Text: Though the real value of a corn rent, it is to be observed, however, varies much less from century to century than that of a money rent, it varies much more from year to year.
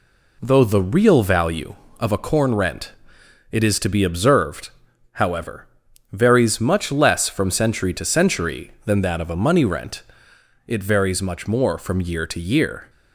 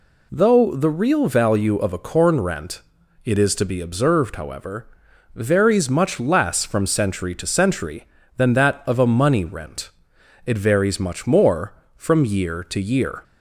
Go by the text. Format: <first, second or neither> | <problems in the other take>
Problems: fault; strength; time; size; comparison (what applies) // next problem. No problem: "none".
neither | none